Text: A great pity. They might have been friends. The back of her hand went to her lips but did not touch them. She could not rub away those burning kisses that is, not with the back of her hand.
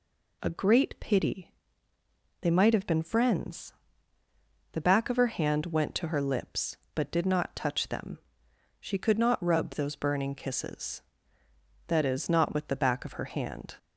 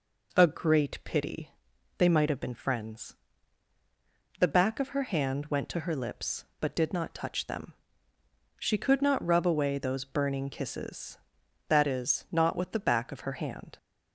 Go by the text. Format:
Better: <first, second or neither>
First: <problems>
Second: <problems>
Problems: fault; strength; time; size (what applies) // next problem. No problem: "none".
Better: second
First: skips "away"; at 9.6 s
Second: none